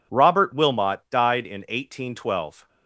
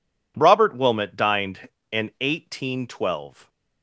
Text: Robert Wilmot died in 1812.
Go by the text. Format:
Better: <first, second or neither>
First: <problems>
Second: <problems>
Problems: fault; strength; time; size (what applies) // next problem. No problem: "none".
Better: first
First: none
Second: says "dined" for "died"; at 1.1 s